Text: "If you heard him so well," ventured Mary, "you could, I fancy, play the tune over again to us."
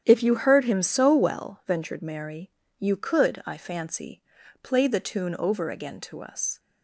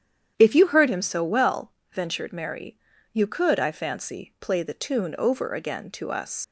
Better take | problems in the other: first | starts louder than the rest; strong; until 1.3 s; 9.5 dB; strong in the first // leaves "us" unfinished; at 6.4 s; 100 ms

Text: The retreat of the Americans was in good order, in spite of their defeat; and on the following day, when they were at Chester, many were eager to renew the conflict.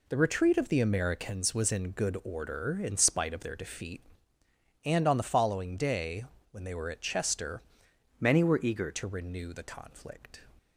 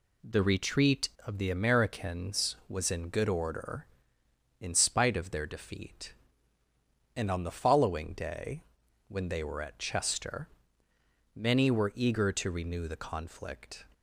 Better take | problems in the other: second | changes voice from "many" to "eager"; from 8.1 to 8.9 s; 0.8 s long

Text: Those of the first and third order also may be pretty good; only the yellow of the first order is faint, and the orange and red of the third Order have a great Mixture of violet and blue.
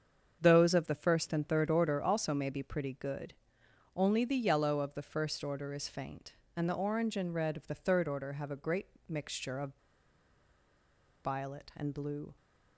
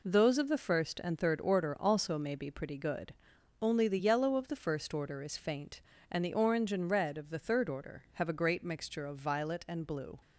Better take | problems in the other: second | starts louder than the rest; strong; until 1.4 s; 7 dB // pauses between "great" and "Mixture"; slight; at 8.8 s; 0.20 s long // pauses between "of" and "violet"; strong; at 9.7 s; 1.5 s long

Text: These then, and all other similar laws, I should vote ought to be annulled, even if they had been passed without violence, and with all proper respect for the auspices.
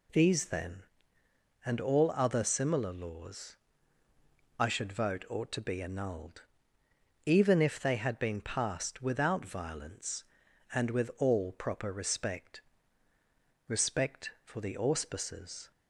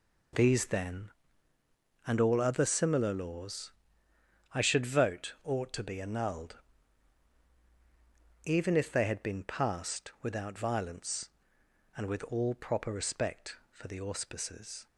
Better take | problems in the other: second | says "respect" twice; at 13.6 s

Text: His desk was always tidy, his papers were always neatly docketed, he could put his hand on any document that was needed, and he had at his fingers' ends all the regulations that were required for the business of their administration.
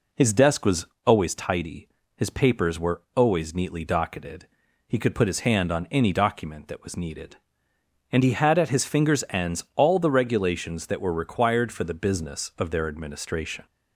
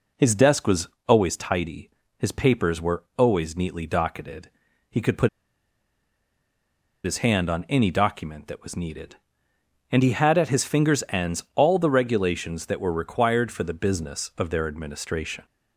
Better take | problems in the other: first | pauses between "was" and "always"; slight; at 0.8 s; 0.20 s long; slight in the first // pauses between "put" and "his"; strong; at 5.2 s; 1.7 s long

